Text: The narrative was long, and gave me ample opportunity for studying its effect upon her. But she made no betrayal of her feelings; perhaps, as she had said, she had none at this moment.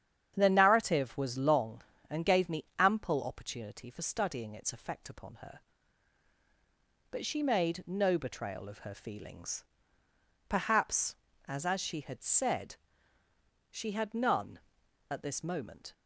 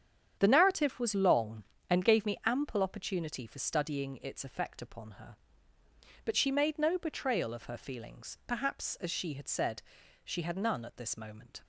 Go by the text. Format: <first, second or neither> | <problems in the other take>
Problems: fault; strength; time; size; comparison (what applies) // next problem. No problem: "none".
second | starts louder than the rest; strong; until 1.3 s; 9 dB; strong in the second // says "as" twice; at 11.6 s